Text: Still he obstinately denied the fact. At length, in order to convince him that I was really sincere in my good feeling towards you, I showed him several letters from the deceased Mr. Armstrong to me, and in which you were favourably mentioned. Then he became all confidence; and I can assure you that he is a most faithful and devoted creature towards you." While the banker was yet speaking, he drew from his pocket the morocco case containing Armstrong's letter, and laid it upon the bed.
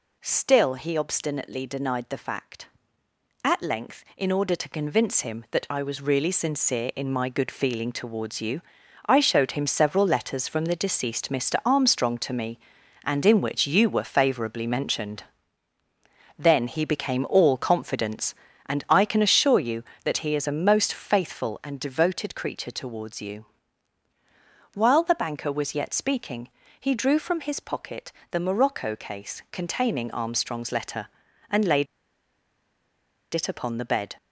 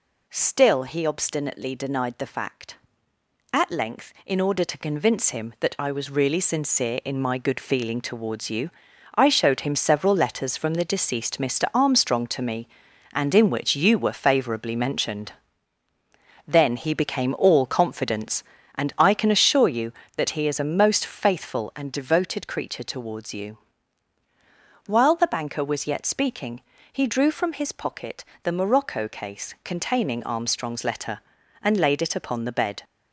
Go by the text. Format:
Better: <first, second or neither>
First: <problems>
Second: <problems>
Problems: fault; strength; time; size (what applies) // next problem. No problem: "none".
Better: second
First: pauses between "pocket" and "the"; slight; at 28.1 s; 0.18 s long // pauses between "laid" and "it"; strong; at 31.8 s; 1.4 s long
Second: pauses between "pocket" and "the"; slight; at 28.2 s; 0.18 s long